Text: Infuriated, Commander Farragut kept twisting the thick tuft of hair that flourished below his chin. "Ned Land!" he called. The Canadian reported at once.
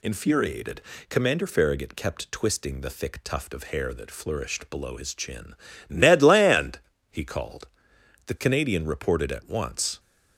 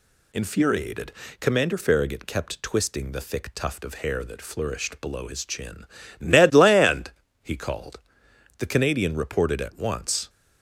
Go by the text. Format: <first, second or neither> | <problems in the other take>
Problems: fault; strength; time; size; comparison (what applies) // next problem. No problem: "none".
neither | none